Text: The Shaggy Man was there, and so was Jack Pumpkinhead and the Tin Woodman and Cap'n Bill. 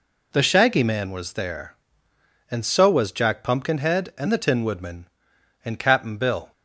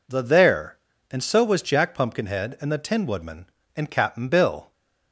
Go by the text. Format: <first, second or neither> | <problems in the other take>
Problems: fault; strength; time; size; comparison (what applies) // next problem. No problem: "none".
first | skips "Shaggy Man was"; at 0.2 s